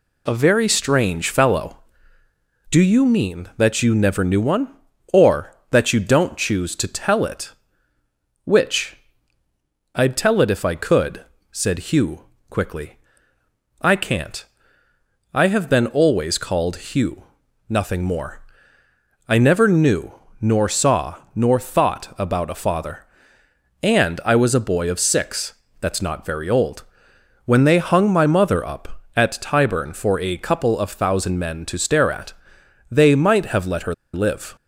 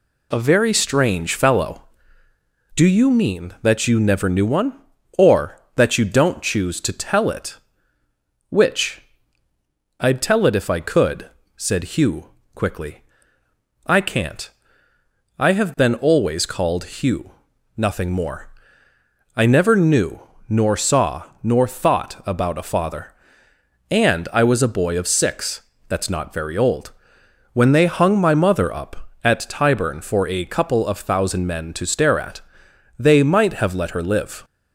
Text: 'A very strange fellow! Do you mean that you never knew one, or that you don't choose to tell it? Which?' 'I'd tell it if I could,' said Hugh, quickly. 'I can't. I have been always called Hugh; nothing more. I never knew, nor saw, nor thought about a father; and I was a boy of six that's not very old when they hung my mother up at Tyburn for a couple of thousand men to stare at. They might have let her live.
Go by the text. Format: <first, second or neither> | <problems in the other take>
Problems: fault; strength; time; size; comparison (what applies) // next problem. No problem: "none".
second | pauses between "six" and "that's"; slight; at 25.5 s; 0.26 s long; slight in the second // pauses between "old" and "when"; noticeable; at 26.8 s; 0.62 s long; noticeable in the second // pauses between "her" and "live"; slight; at 33.9 s; 0.19 s long